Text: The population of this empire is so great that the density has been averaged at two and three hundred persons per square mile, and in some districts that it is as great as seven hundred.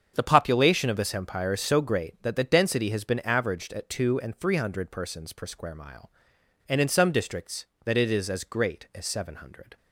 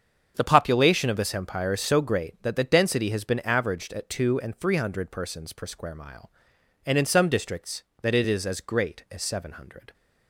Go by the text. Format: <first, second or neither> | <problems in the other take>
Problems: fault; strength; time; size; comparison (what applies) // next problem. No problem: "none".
neither | starts louder than the rest; strong; the same in both